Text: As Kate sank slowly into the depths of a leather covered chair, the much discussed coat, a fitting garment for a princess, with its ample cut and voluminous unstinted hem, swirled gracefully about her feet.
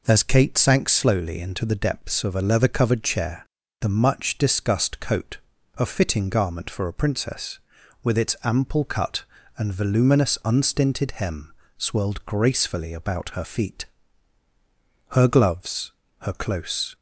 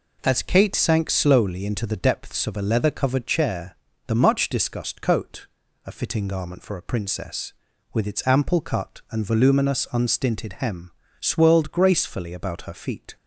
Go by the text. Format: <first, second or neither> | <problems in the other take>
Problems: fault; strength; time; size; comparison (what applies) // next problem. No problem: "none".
second | goes on to say "Her gloves her close"; strong; from 15.1 s on; 1.8 s long